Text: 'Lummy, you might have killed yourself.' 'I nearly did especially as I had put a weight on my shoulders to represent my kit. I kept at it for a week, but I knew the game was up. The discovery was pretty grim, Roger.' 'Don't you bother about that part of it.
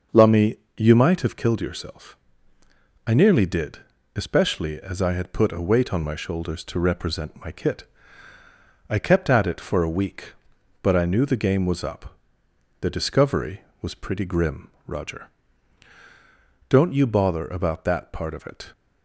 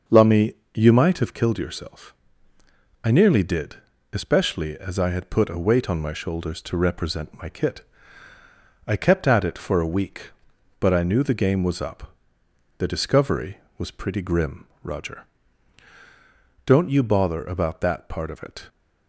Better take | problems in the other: neither | starts louder than the rest; the same in both // pauses between "did" and "especially"; slight; the same in both

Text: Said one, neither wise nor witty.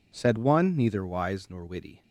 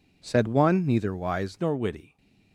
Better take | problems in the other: first | changes voice at "nor"; from 1.6 s on; 0.5 s long

